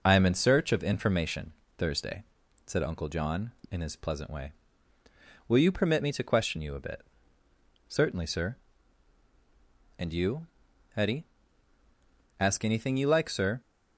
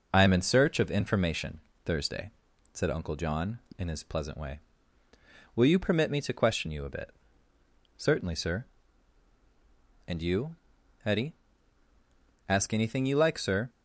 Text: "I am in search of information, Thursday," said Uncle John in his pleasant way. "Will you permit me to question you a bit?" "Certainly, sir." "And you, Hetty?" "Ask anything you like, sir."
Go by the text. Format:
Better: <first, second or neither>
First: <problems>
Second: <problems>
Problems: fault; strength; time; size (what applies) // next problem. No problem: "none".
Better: neither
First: none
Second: none